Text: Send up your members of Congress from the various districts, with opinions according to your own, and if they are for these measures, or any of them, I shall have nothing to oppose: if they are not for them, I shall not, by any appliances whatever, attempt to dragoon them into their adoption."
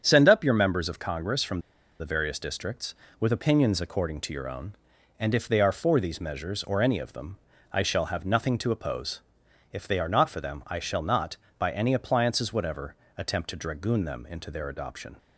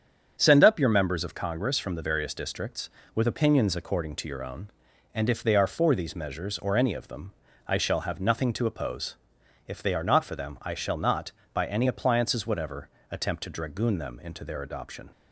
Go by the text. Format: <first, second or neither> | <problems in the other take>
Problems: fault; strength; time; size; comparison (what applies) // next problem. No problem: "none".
second | starts louder than the rest; strong; until 1.0 s; 7.5 dB; strong in the second // pauses between "from" and "the"; at 1.5 s; 0.39 s long